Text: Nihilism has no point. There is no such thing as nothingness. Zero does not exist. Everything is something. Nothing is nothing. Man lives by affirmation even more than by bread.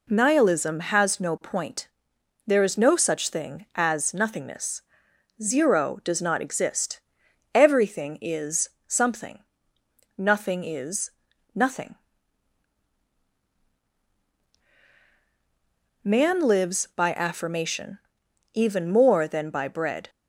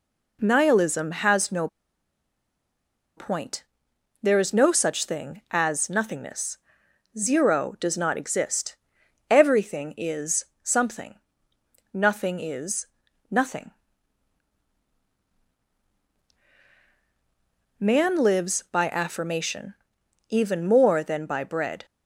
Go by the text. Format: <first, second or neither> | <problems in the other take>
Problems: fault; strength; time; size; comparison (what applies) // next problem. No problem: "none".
first | pauses between "no" and "point"; strong; at 1.6 s; 1.4 s long // pauses between "is" and "something"; slight; at 10.4 s; 0.18 s long; slight in the first // pauses between "is" and "nothing"; at 12.8 s; 0.44 s long; also in the first // pauses between "affirmation" and "even"; noticeable; at 19.7 s; 0.56 s long; noticeable in the first